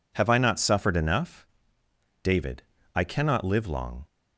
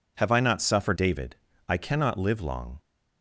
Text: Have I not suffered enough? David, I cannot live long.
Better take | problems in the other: first | skips "enough"; at 0.9 s

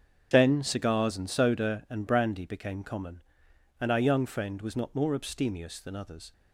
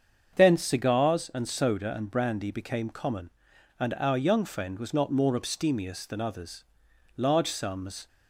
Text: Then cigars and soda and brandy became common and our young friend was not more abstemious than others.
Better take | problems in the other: first | starts louder than the rest; until 1.4 s; 7 dB; strong in the first // goes on to say "Large sums"; noticeable; from 7.1 s on; 0.90 s long

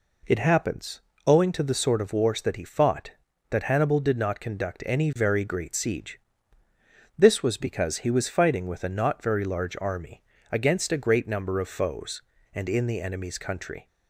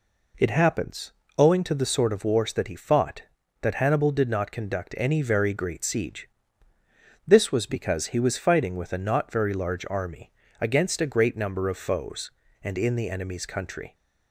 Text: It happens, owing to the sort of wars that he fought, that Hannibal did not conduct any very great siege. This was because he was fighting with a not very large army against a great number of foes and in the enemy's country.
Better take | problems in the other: neither | pauses between "army" and "against"; slight; the same in both

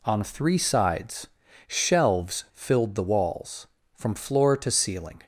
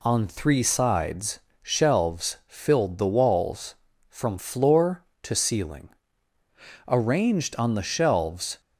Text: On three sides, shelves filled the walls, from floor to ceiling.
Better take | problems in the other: first | goes on to say "Arranged on the shelves"; strong; from 6.8 s on; 1.7 s long

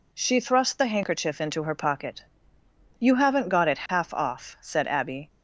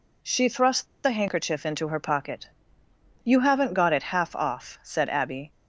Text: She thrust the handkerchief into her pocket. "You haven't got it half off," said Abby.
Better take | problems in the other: first | pauses between "thrust" and "the"; slight; at 0.8 s; 0.18 s long

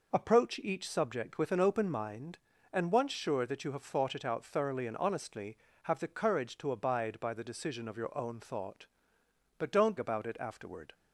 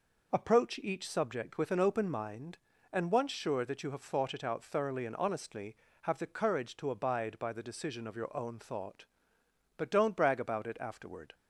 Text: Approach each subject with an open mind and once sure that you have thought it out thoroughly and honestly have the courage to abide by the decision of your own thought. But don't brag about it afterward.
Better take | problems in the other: second | skips "brag"; at 9.9 s

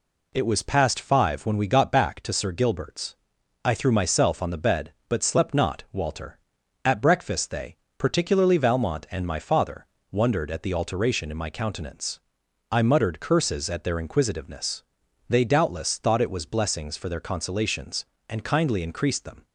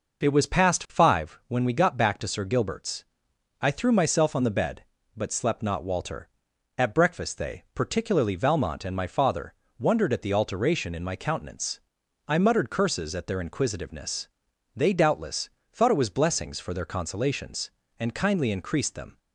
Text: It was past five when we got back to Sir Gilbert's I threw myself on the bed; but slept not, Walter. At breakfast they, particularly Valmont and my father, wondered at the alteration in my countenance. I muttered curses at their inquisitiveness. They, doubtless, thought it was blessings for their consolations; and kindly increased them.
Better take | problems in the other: first | starts louder than the rest; noticeable; until 1.4 s; 5.5 dB // pauses between "Gilbert's" and "I"; noticeable; at 3.0 s; 0.58 s long; noticeable in the first

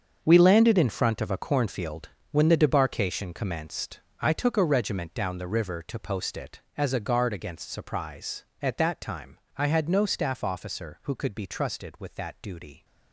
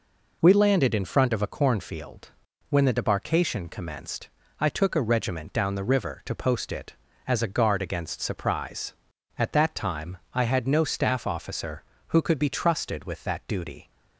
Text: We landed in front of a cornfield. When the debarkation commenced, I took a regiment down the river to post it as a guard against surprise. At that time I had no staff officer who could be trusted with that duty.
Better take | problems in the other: second | gets quieter; strong; throughout; 12.5 dB // pauses between "time" and "I"; slight; at 9.3 s; 0.18 s long; slight in the second

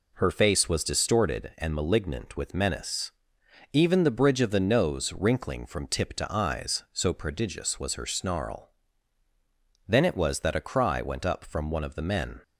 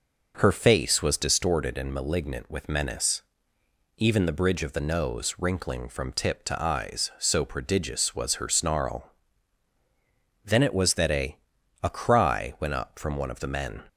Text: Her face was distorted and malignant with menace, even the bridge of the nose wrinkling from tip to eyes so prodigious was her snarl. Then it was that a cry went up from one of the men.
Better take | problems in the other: first | says "a" twice; at 11.8 s

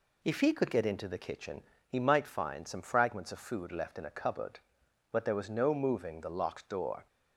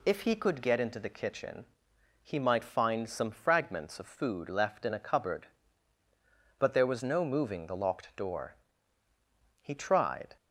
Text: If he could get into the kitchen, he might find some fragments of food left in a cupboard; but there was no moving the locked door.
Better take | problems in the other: first | goes on to say "He tried"; noticeable; from 9.5 s on; 0.76 s long

